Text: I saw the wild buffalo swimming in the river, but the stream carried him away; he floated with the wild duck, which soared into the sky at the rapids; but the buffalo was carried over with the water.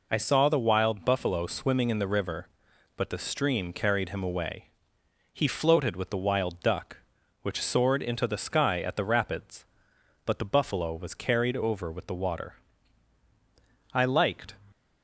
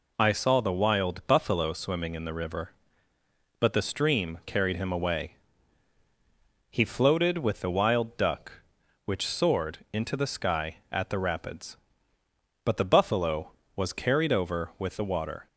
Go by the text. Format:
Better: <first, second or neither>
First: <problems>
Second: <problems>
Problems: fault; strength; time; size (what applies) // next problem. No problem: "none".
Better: second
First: goes on to say "I liked"; noticeable; from 13.9 s on; 0.62 s long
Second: none